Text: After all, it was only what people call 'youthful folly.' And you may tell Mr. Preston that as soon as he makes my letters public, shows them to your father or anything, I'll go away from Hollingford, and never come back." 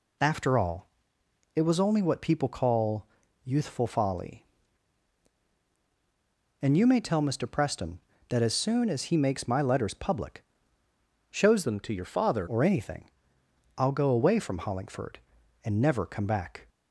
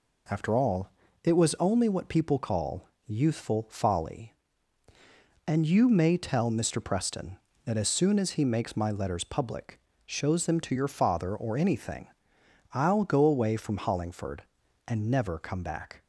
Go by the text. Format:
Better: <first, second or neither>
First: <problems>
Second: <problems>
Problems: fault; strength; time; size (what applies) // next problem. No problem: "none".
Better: second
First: pauses between "call" and "youthful"; at 3.0 s; 0.38 s long // changes voice from "them" to "father"; from 11.6 to 12.4 s; 0.8 s long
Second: pauses between "call" and "youthful"; slight; at 2.8 s; 0.18 s long